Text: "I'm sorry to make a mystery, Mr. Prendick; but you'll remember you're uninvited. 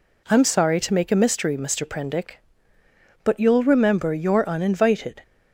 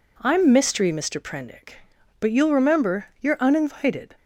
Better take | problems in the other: first | skips "sorry to make a"; at 0.5 s // pauses between "remember" and "you're"; slight; at 3.0 s; 0.16 s long

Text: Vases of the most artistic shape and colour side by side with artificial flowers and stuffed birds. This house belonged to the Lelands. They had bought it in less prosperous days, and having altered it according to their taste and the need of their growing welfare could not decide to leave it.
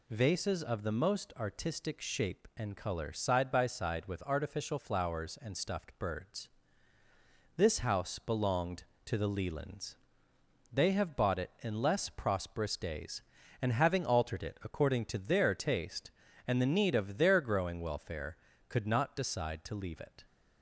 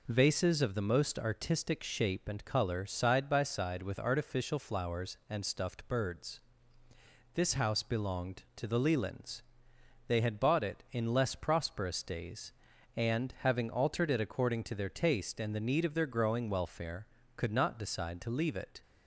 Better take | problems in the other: second | says "have" for "had"; at 10.9 s

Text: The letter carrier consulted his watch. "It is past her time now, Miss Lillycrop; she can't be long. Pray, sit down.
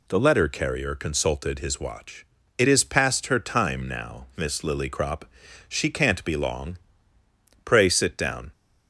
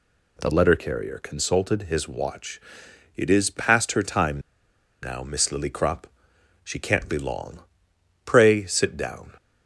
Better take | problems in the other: first | pauses between "time" and "now"; noticeable; at 4.3 s; 0.62 s long

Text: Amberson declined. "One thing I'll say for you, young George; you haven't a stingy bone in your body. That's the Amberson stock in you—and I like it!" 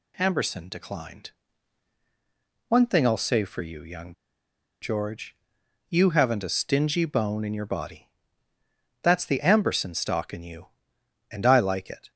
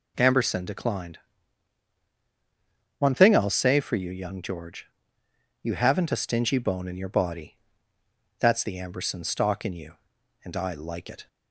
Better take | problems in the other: second | pauses between "young" and "George"; noticeable; at 4.1 s; 0.68 s long

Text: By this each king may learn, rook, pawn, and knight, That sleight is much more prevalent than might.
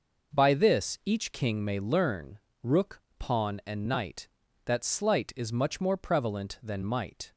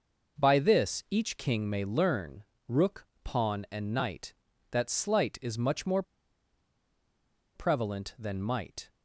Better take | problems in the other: first | pauses between "more" and "prevalent"; strong; at 6.0 s; 1.5 s long

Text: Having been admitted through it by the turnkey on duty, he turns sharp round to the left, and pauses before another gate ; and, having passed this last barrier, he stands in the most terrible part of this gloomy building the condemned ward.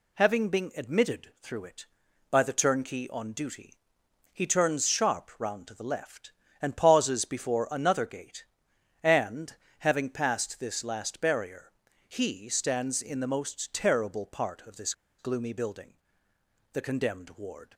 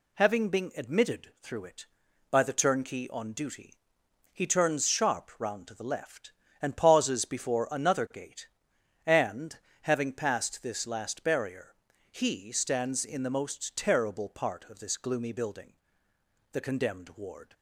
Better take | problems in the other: second | pauses between "this" and "gloomy"; slight; at 14.9 s; 0.26 s long // pauses between "building" and "the"; noticeable; at 15.9 s; 0.80 s long; noticeable in the second

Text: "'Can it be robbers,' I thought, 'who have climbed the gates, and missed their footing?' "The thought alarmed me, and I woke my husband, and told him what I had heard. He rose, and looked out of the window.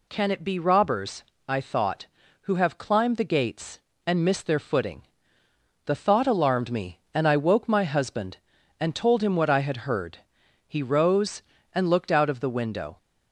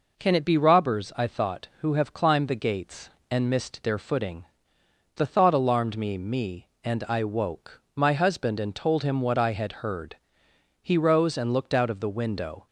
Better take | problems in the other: first | says "me" twice; at 6.1 s // pauses between "woke" and "my"; slight; at 7.8 s; 0.16 s long

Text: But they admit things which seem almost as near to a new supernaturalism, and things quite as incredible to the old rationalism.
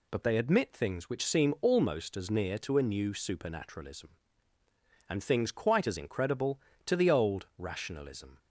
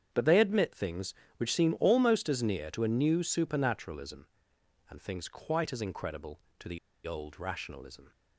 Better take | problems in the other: first | starts louder than the rest; strong; until 1.1 s; 8 dB // pauses between "the" and "old"; slight; at 6.7 s; 0.28 s long

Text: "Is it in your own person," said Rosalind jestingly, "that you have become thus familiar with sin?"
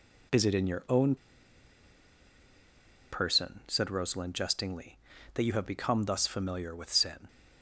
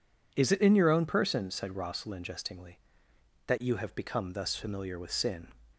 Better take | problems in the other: second | pauses between "own" and "person"; strong; at 1.1 s; 1.9 s long

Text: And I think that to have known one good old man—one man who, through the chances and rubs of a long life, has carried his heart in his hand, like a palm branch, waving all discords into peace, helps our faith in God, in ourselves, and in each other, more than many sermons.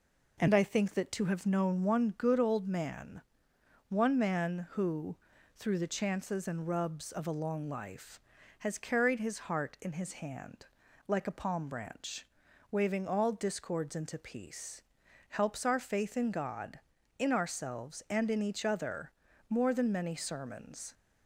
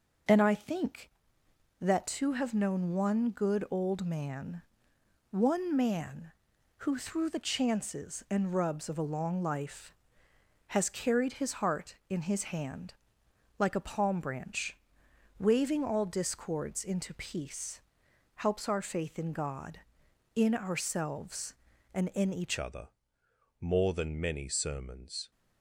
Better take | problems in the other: first | starts louder than the rest; noticeable; until 1.9 s; 6 dB // changes voice at "other"; from 22.5 s on; 2.8 s long

